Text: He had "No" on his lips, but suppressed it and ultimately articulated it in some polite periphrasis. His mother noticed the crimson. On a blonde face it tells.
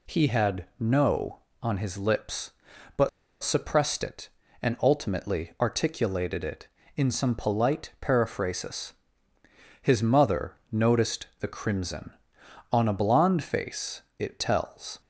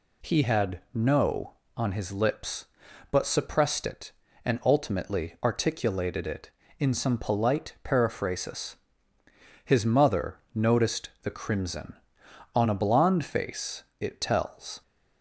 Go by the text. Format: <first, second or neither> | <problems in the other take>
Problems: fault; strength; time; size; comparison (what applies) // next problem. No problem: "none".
second | pauses between "but" and "suppressed"; slight; at 3.0 s; 0.32 s long // pauses between "mother" and "noticed"; slight; at 10.5 s; 0.16 s long; slight in the second